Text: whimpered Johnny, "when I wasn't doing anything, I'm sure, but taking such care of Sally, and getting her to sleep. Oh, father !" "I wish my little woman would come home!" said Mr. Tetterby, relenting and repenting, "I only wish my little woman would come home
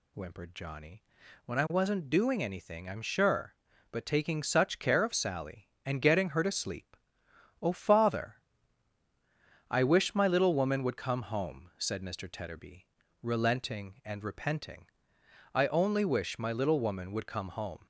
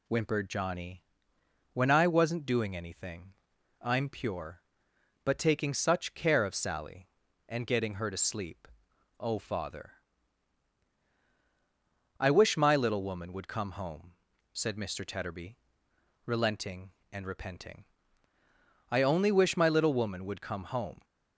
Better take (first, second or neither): first